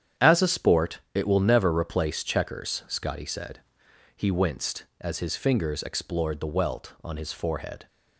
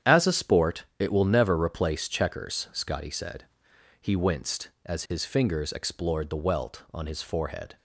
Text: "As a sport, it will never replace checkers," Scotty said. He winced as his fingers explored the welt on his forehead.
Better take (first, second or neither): neither